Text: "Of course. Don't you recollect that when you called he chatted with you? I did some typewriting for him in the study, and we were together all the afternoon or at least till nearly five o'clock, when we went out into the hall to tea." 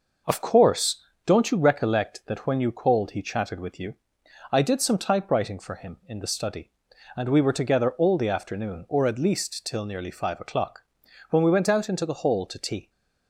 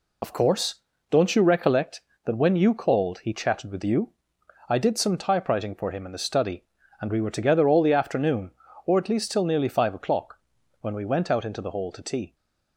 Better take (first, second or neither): first